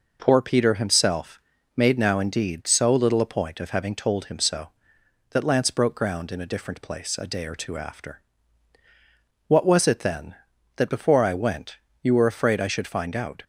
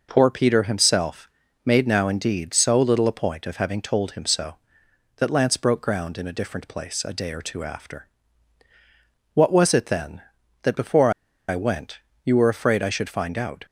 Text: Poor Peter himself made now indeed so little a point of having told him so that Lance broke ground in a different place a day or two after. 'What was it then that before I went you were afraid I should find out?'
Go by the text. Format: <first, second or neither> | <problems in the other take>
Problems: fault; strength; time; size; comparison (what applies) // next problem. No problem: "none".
first | pauses between "himself" and "made"; slight; at 1.2 s; 0.34 s long; slight in the first // pauses between "before" and "I"; at 11.1 s; 0.36 s long // pauses between "went" and "you"; slight; at 11.9 s; 0.26 s long; slight in the first